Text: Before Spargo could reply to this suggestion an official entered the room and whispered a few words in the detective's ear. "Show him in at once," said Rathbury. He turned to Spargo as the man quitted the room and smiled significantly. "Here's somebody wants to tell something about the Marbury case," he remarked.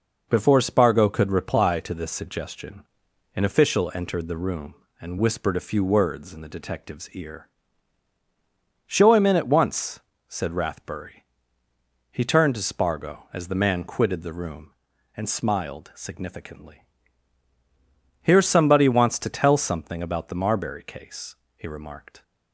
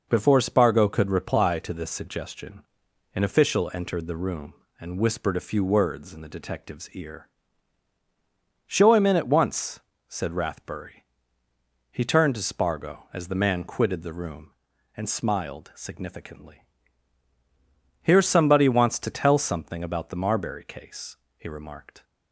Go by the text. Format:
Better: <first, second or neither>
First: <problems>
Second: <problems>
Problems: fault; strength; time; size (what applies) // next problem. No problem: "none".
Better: neither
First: pauses between "suggestion" and "an"; noticeable; at 2.8 s; 0.52 s long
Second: pauses between "suggestion" and "an"; noticeable; at 2.6 s; 0.52 s long